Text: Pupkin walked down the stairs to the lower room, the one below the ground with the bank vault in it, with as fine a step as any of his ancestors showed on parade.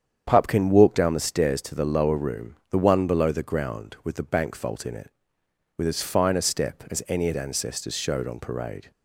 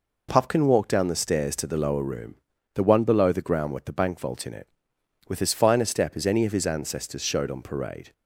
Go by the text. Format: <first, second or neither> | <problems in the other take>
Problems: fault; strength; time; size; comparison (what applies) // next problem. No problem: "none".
second | starts louder than the rest; strong; until 1.2 s; 8 dB // skips "his"; at 7.3 s